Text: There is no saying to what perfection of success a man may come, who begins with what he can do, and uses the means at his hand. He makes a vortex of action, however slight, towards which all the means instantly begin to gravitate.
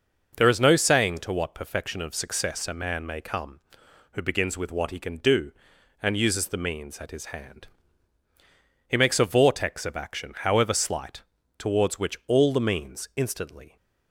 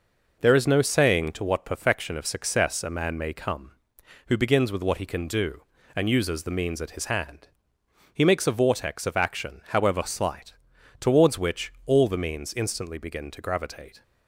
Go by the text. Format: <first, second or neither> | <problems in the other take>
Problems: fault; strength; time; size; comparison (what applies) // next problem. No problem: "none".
second | stops before "begin to gravitate"; at 13.7 s